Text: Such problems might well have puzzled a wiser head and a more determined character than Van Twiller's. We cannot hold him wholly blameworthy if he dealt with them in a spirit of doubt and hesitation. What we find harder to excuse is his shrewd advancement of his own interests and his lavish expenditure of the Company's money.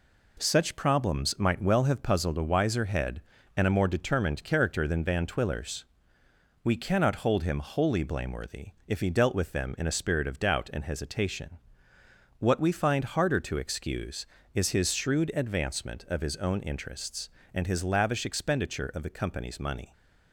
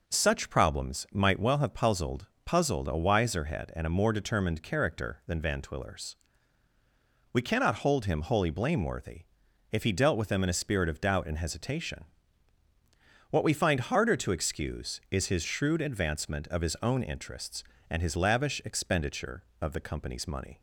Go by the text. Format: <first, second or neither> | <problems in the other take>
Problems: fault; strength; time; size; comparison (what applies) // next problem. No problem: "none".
first | says "puzzled" twice; at 2.4 s // pauses between "blameworthy" and "if"; noticeable; at 9.2 s; 0.48 s long; slight in the first